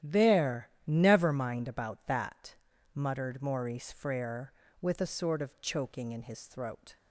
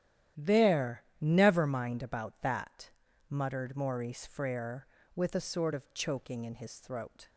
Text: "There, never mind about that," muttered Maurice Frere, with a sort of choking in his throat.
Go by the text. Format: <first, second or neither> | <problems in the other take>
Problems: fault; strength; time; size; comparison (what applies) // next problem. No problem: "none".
neither | starts louder than the rest; strong; the same in both